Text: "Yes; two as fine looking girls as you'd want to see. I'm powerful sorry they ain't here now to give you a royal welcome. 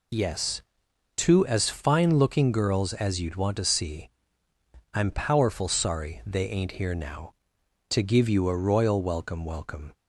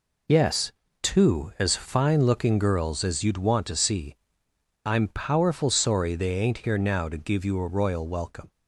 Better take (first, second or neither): second